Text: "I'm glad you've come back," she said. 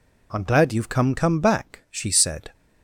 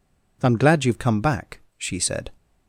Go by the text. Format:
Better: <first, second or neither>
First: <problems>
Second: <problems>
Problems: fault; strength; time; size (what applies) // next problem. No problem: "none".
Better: second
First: says "come" twice; at 1.1 s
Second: none